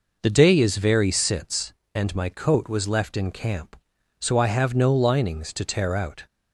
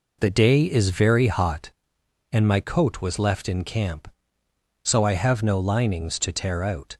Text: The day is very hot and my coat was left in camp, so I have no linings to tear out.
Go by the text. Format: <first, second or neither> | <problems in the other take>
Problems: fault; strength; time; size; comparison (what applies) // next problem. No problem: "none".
second | says "sits" for "hot"; at 1.1 s